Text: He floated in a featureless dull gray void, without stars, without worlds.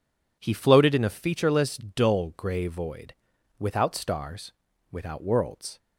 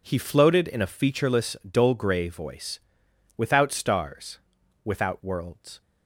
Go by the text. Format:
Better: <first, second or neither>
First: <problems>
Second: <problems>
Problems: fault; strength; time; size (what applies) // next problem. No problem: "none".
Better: first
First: none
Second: says "voice" for "void"; at 2.2 s